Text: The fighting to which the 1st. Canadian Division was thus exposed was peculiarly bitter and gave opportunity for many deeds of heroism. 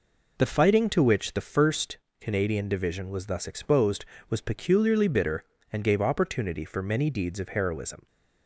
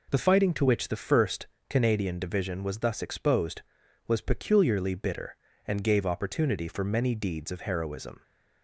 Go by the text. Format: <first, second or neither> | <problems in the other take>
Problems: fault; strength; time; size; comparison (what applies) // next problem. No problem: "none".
neither | none